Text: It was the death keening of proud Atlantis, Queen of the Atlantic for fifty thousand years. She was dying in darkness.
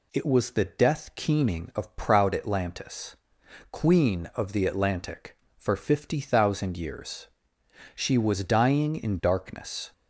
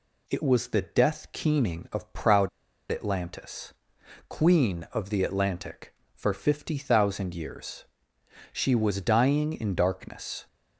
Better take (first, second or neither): first